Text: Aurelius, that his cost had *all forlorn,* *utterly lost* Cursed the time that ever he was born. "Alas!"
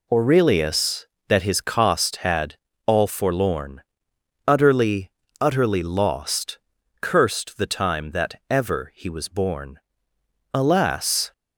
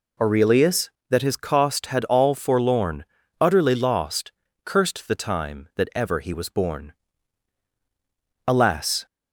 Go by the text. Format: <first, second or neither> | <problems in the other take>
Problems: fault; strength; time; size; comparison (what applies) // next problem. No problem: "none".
second | pauses between "had" and "all"; slight; at 2.5 s; 0.30 s long // says "utterly" twice; at 5.3 s // pauses between "lost" and "Cursed"; at 6.5 s; 0.42 s long; slight in the second